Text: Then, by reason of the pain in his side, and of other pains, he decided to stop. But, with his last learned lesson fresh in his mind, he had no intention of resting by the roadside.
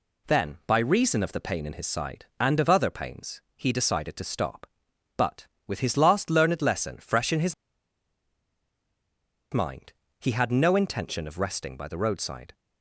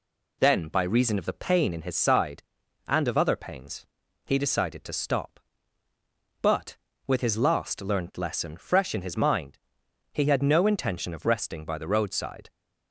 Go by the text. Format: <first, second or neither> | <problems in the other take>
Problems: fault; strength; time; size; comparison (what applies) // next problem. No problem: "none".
second | pauses between "his" and "mind"; strong; at 7.5 s; 1.9 s long